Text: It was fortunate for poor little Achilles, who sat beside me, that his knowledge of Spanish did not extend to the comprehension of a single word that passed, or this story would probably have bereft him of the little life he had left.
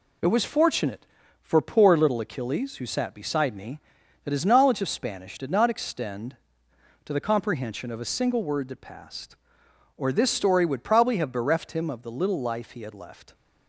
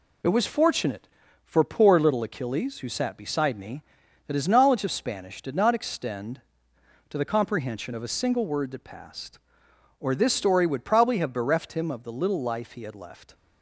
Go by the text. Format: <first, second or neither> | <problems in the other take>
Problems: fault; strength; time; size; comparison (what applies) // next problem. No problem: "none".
neither | none